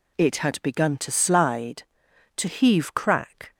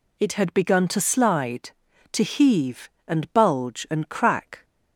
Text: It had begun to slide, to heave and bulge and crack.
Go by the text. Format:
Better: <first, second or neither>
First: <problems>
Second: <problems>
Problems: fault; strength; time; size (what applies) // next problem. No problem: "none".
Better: second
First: skips "and bulge and"; at 2.9 s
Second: none